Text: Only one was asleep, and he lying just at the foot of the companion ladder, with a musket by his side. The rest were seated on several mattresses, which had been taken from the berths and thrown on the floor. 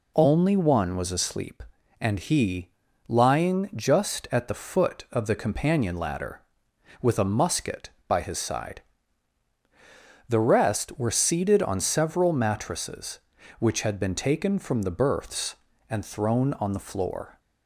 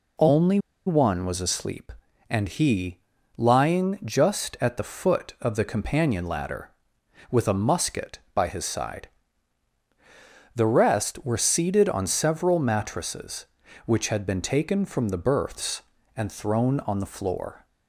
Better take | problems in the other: first | pauses between "Only" and "one"; slight; at 0.5 s; 0.27 s long // pauses between "he" and "lying"; slight; at 2.9 s; 0.36 s long; slight in the first

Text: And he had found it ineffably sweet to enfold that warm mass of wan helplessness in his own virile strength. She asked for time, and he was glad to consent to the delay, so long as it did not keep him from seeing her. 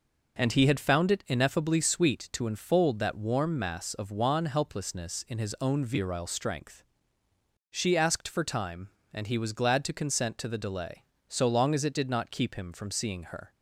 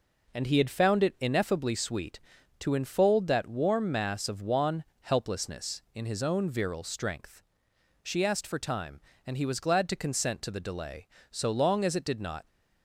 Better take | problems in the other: first | pauses between "wan" and "helplessness"; slight; at 4.8 s; 0.18 s long // stops before "keep him from seeing her"; at 12.4 s

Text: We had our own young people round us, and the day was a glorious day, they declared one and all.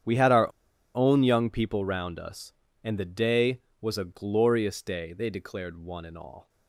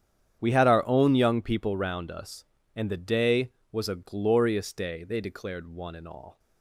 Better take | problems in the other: second | starts louder than the rest; strong; until 1.4 s; 9 dB; strong in the second // pauses between "our" and "own"; at 0.5 s; 0.43 s long

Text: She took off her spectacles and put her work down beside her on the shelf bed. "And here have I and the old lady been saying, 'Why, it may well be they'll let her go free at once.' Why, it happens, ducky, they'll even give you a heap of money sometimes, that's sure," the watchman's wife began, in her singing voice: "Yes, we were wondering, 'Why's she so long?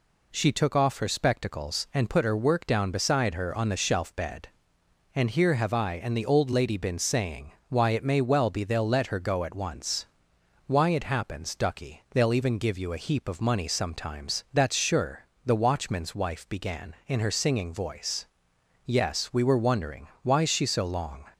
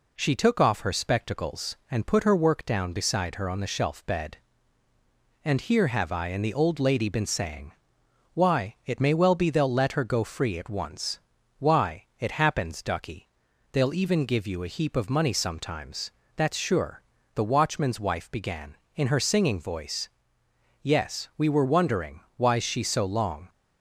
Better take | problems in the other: second | skips "free"; at 9.4 s

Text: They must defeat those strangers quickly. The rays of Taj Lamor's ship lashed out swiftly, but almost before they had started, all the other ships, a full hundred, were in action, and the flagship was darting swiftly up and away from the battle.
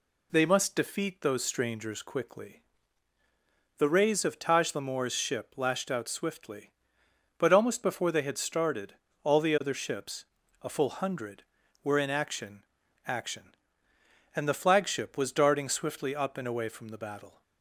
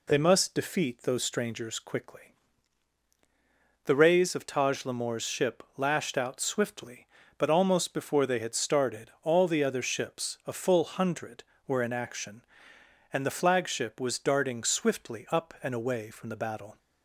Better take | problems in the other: second | says "action" twice; at 13.0 s

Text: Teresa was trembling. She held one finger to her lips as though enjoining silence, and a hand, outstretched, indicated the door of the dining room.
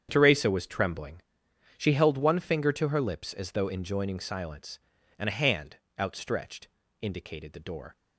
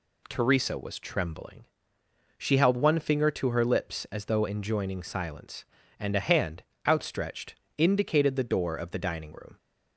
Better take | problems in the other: second | starts louder than the rest; strong; until 1.1 s; 8.5 dB // stops before "of the dining room"; at 7.9 s

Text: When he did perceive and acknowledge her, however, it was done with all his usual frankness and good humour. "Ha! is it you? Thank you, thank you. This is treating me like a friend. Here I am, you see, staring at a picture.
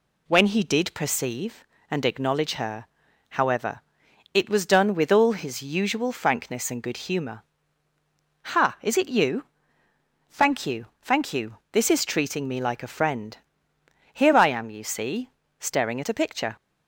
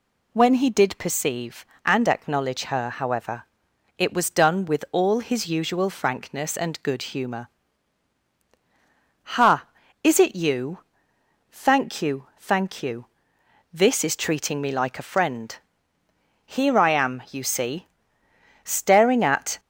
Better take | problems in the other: first | stops before "a picture"; at 19.5 s

